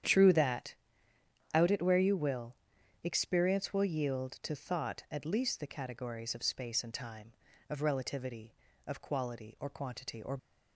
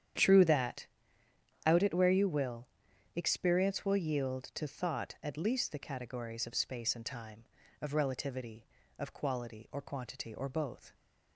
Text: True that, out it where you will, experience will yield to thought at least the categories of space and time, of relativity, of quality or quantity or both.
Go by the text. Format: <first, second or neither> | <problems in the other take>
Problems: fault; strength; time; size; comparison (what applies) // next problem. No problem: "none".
second | starts louder than the rest; strong; until 1.8 s; 9.5 dB; strong in the second // stops before "both"; at 10.3 s